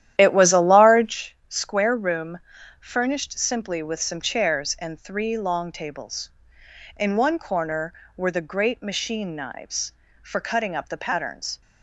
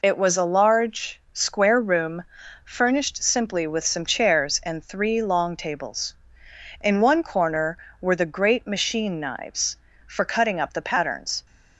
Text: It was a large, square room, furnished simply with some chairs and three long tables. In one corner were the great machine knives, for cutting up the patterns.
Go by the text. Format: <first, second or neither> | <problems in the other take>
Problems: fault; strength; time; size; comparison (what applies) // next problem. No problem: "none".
second | starts louder than the rest; strong; until 1.2 s; 11.5 dB